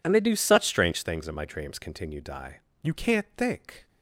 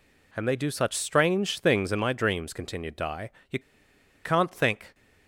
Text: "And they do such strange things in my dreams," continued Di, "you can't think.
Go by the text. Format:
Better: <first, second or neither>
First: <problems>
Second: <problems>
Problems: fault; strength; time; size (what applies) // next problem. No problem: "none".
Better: first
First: none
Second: pauses between "you" and "can't"; noticeable; at 3.5 s; 0.65 s long